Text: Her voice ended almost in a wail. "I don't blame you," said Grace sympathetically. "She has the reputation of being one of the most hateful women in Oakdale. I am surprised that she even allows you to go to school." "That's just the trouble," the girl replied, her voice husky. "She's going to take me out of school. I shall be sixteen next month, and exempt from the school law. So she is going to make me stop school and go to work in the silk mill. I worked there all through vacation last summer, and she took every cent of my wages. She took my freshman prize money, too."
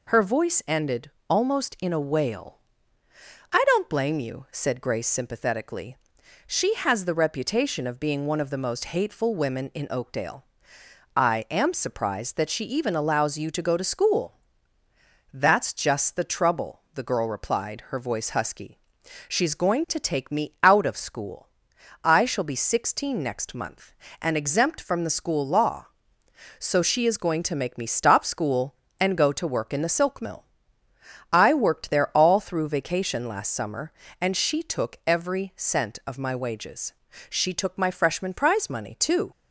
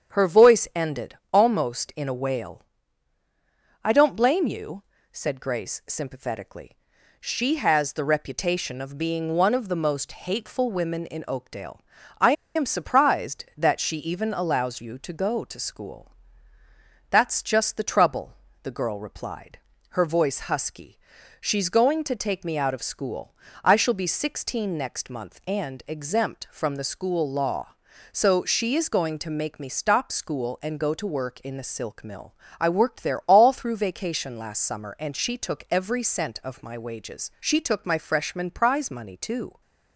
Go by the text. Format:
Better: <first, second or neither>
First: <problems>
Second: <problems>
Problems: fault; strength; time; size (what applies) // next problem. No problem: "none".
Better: first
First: pauses between "ended" and "almost"; slight; at 1.0 s; 0.18 s long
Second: starts louder than the rest; strong; until 1.3 s; 8 dB // pauses between "ended" and "almost"; slight; at 1.1 s; 0.16 s long // pauses between "I" and "am"; slight; at 12.3 s; 0.23 s long